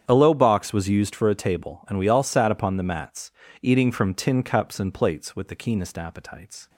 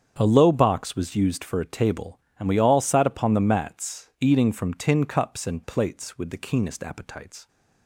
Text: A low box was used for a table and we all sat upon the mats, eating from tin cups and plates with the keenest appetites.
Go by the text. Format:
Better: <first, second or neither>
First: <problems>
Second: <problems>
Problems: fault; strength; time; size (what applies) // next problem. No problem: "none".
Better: neither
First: starts louder than the rest; strong; until 1.0 s; 8.5 dB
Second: starts louder than the rest; strong; until 1.1 s; 8 dB